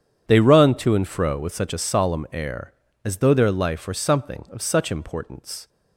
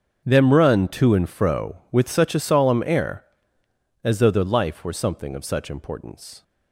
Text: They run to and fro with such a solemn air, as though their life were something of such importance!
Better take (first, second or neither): first